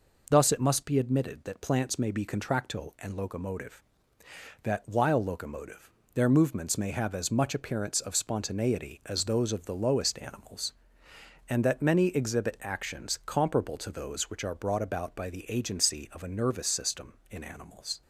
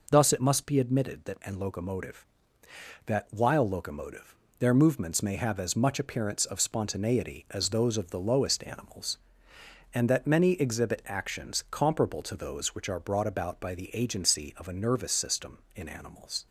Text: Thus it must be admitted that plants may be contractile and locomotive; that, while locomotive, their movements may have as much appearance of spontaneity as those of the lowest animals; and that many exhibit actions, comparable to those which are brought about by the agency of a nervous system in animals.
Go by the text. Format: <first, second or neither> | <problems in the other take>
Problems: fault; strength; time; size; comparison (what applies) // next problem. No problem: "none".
first | skips "plants may be contractile"; at 1.4 s